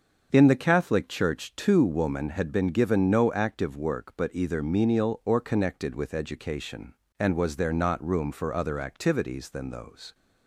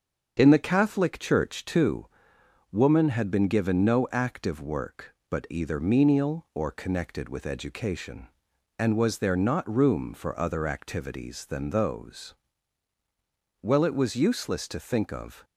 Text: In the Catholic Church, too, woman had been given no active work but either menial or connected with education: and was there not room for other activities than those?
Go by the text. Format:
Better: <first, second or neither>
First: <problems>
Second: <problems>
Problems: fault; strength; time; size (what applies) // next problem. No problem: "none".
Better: first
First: starts louder than the rest; until 1.3 s; 6.5 dB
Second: starts louder than the rest; until 1.3 s; 7 dB // goes on to say "Well it was useless to think of"; strong; from 13.6 s on; 1.8 s long